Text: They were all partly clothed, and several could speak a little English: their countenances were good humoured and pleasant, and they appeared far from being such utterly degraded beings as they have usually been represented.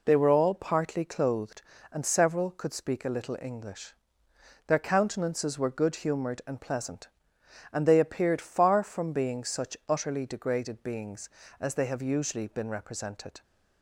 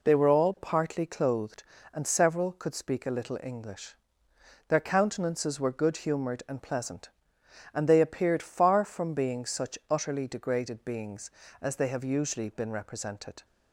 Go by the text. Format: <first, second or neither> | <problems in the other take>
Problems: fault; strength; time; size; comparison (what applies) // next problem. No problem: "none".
neither | none